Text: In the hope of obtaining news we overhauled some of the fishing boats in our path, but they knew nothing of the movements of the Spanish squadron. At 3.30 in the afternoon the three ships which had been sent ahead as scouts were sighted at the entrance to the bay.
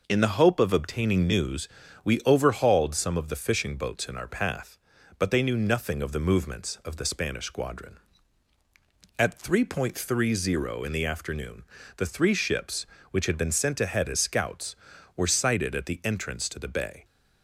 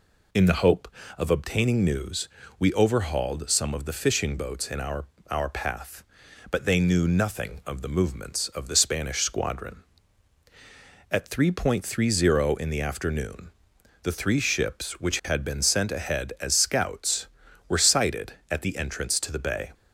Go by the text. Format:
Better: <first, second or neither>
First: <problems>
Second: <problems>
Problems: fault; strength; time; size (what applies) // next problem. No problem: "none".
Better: first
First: pauses between "news" and "we"; at 1.6 s; 0.38 s long // pauses between "afternoon" and "the"; slight; at 11.6 s; 0.32 s long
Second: pauses between "news" and "we"; slight; at 2.2 s; 0.28 s long // says "our" twice; at 5.2 s // pauses between "afternoon" and "the"; noticeable; at 13.5 s; 0.52 s long